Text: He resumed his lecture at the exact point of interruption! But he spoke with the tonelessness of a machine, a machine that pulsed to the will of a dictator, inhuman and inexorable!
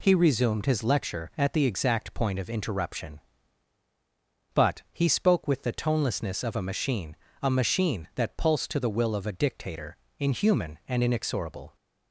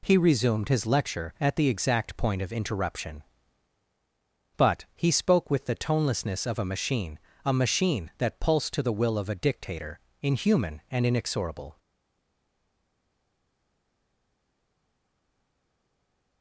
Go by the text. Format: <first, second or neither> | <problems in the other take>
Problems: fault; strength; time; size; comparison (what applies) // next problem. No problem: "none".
first | stays silent after the last word; strong; from 11.7 s on; 4.7 s long